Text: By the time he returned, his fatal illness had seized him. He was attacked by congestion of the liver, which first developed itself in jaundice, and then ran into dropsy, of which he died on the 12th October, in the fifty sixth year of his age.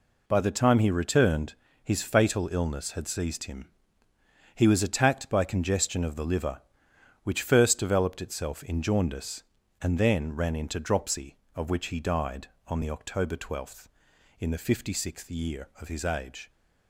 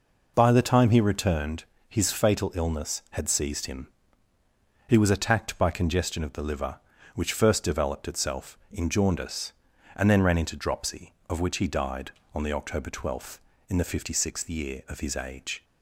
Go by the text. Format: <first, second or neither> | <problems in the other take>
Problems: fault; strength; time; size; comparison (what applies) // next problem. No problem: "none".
neither | none